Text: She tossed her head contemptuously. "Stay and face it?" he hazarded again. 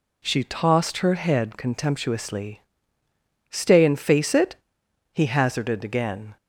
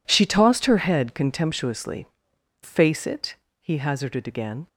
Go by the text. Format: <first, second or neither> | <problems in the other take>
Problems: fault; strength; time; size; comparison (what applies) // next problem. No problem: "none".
first | skips "Stay and"; at 2.3 s